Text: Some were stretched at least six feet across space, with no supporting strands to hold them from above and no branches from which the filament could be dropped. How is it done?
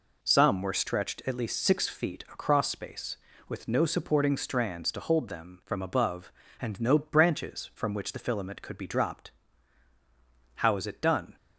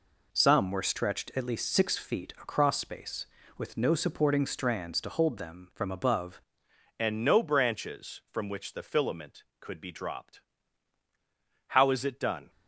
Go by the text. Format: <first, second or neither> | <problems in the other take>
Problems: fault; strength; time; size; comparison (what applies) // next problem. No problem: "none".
first | changes voice at "and"; from 6.9 s on; 5.5 s long